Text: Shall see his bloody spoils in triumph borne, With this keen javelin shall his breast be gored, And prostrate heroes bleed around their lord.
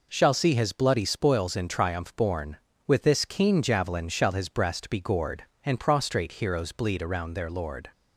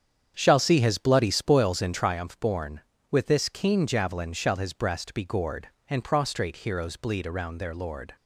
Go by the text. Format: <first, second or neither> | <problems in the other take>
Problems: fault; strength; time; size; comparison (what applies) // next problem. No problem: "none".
first | starts louder than the rest; strong; until 2.2 s; 8.5 dB